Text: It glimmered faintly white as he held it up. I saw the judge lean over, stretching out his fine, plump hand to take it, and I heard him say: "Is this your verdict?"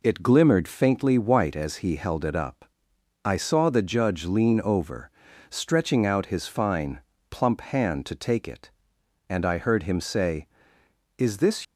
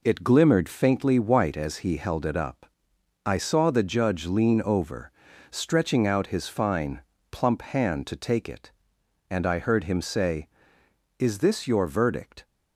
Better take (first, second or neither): second